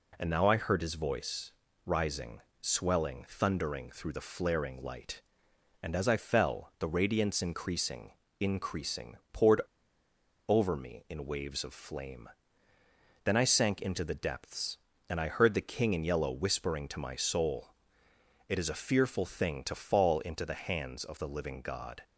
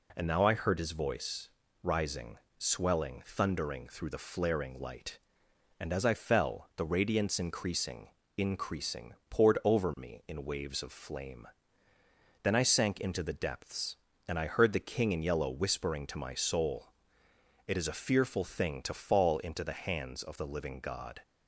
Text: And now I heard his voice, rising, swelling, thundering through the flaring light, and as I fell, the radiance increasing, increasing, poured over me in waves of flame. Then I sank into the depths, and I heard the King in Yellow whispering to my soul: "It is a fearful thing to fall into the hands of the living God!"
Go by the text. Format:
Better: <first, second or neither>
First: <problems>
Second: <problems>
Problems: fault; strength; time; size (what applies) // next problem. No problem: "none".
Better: second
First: pauses between "poured" and "over"; noticeable; at 9.5 s; 0.88 s long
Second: none